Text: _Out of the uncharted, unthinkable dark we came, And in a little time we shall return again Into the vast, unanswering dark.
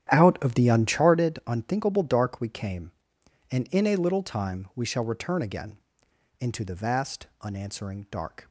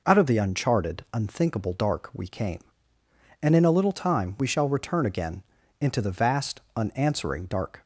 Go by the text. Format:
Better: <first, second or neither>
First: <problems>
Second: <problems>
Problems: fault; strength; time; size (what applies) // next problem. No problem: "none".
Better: second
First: starts louder than the rest; strong; until 1.2 s; 10.5 dB // pauses between "again" and "Into"; noticeable; at 5.7 s; 0.62 s long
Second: pauses between "again" and "Into"; at 5.4 s; 0.38 s long